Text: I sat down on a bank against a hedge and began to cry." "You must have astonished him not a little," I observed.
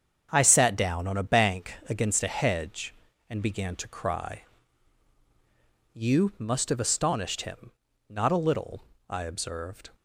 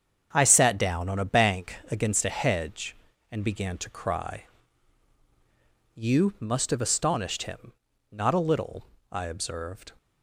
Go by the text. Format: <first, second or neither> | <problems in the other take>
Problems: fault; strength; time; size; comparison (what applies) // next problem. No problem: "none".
neither | starts louder than the rest; strong; the same in both // pauses between "him" and "not"; the same in both